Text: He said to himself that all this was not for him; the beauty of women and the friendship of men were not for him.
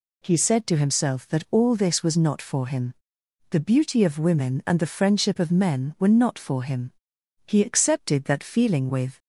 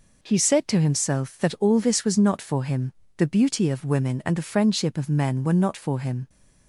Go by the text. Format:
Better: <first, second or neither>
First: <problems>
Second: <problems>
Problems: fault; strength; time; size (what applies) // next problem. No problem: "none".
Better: second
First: goes on to say "He accepted that feeling with"; strong; from 7.4 s on; 1.7 s long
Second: none